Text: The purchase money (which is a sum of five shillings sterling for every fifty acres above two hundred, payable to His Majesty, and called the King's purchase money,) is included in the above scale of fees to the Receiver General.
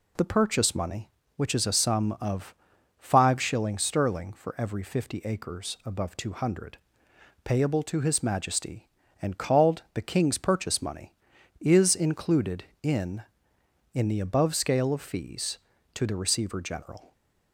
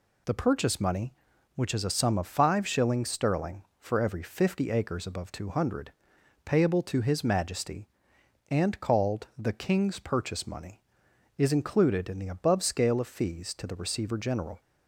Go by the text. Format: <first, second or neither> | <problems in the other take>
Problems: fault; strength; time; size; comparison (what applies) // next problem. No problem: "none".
second | pauses between "of" and "five"; at 2.5 s; 0.44 s long // says "in" twice; at 13.9 s